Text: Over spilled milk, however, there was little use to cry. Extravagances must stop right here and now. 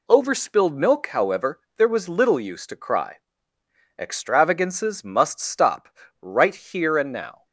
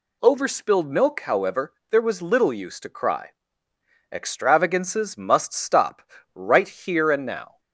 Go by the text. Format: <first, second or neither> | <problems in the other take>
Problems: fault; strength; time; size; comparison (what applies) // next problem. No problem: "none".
second | gets quieter; throughout; 7 dB // pauses between "stop" and "right"; slight; at 5.8 s; 0.32 s long; slight in the second